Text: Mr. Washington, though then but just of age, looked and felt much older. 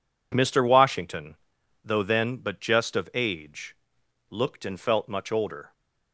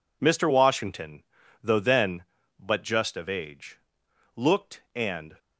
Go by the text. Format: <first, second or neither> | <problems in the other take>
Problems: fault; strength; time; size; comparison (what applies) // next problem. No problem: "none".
first | stops before "felt much older"; at 5.3 s